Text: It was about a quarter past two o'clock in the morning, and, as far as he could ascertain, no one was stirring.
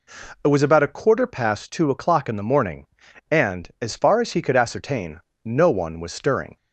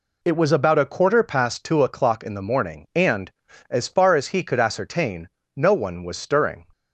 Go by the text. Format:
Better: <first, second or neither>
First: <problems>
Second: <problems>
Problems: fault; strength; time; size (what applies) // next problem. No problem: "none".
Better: neither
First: none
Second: none